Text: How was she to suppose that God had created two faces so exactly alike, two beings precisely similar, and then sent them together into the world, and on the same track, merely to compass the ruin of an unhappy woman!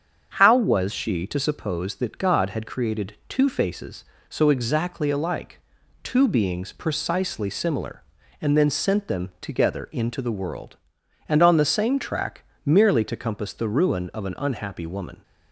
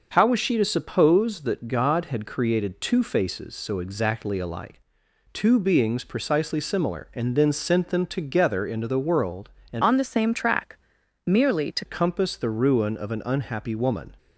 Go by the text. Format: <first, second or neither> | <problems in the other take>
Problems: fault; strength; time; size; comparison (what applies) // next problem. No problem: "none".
first | starts louder than the rest; noticeable; until 1.1 s; 6 dB; strong in the first // changes voice from "on" to "to"; from 9.8 to 11.8 s; 2.0 s long